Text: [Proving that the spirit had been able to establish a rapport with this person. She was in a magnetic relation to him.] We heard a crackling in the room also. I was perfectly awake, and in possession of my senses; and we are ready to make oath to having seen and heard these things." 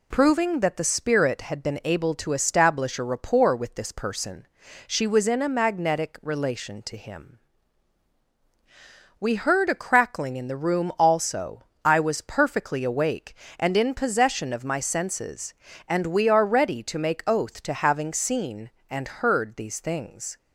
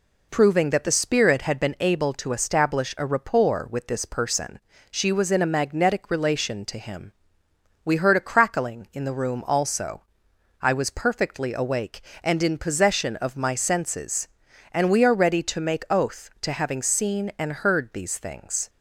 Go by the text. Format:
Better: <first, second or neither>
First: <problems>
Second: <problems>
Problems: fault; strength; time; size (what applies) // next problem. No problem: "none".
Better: neither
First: none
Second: none